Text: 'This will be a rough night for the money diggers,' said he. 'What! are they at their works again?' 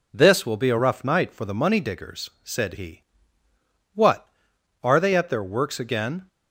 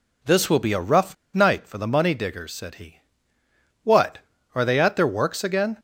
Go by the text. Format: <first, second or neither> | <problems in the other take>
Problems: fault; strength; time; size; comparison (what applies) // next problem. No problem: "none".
first | pauses between "rough" and "night"; slight; at 1.1 s; 0.19 s long